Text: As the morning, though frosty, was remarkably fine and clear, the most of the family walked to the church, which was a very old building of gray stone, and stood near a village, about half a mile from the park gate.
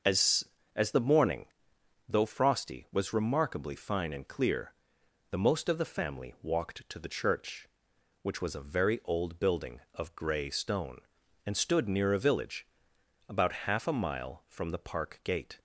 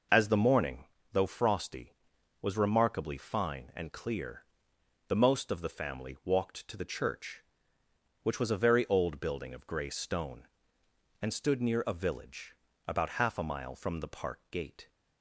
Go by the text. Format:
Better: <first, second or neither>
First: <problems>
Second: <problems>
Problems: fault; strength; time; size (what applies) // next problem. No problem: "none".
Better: second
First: starts louder than the rest; until 1.3 s; 6.5 dB // says "As" twice; at 0.7 s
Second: none